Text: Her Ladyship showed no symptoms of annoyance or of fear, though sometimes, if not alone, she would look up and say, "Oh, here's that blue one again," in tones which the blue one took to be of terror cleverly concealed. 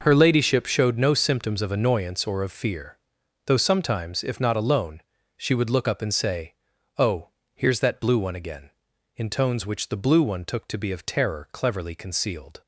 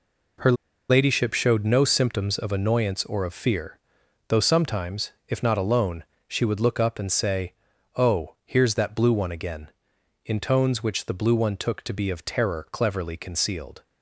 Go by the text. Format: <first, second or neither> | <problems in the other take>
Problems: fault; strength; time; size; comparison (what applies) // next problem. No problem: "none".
first | pauses between "Her" and "Ladyship"; at 0.5 s; 0.36 s long